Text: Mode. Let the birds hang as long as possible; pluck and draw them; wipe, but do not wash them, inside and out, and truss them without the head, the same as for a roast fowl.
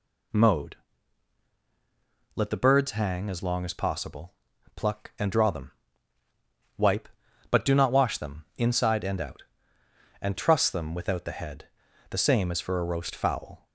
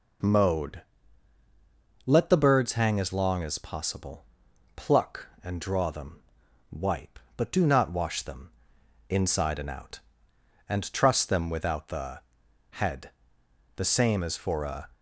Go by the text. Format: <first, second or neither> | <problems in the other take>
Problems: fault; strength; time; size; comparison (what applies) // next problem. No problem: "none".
first | pauses between "the" and "head"; noticeable; at 12.1 s; 0.52 s long // stops before "roast fowl"; at 14.9 s